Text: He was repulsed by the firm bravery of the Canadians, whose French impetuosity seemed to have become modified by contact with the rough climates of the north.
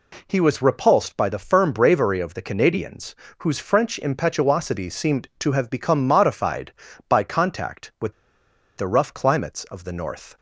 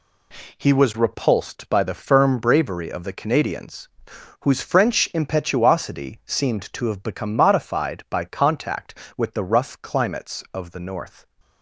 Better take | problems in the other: second | pauses between "with" and "the"; noticeable; at 8.1 s; 0.63 s long

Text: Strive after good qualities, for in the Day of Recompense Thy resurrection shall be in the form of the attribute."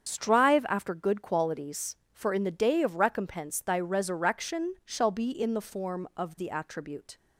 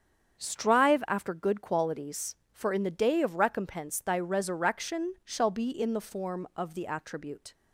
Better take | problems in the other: second | loses the start of "Strive"; at 0.0 s; 45 ms // starts louder than the rest; strong; until 1.1 s; 7.5 dB; strong in the second

